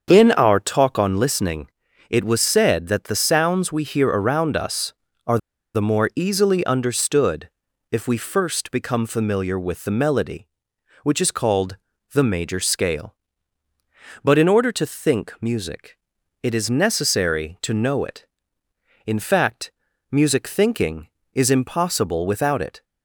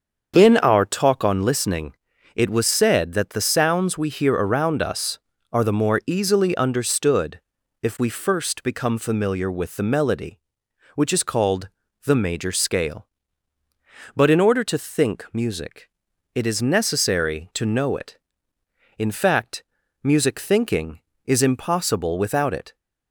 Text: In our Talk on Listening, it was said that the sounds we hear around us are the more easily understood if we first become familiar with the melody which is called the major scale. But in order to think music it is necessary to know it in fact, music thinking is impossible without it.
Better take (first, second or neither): second